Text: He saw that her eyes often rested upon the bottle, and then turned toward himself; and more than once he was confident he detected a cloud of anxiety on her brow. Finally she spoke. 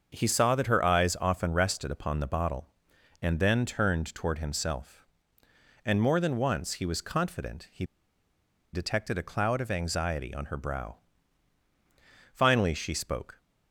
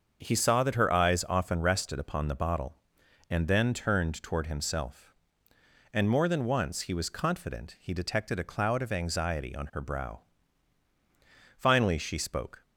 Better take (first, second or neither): second